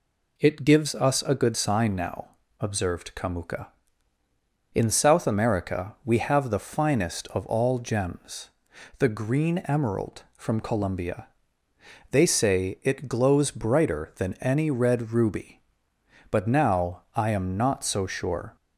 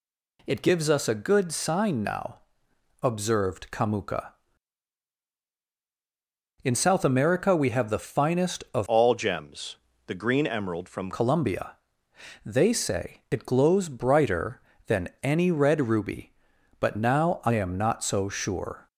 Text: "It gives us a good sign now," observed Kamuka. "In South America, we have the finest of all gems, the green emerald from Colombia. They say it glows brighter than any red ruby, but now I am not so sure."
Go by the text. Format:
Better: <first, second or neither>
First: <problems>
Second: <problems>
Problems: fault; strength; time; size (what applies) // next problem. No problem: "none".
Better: first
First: none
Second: changes voice from "all" to "from"; from 8.8 to 11.1 s; 2.3 s long